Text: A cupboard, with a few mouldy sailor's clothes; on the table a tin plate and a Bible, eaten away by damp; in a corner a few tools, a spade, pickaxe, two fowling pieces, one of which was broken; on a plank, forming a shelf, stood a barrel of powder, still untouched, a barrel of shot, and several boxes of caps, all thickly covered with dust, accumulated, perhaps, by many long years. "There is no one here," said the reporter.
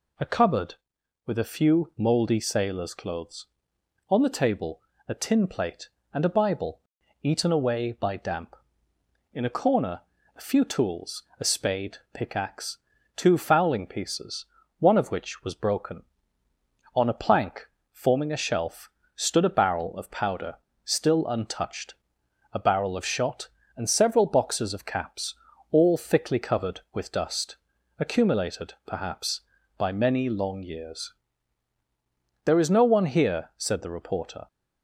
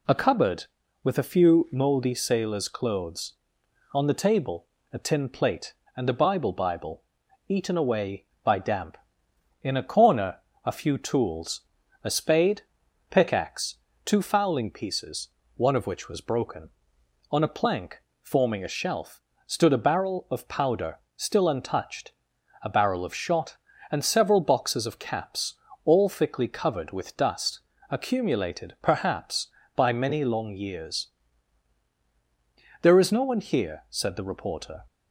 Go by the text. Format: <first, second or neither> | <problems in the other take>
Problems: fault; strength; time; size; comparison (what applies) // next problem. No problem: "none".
first | pauses between "table" and "a"; slight; at 4.6 s; 0.26 s long; slight in the first // says "Bible" twice; at 6.5 s // pauses between "corner" and "a"; slight; at 10.3 s; 0.26 s long; slight in the first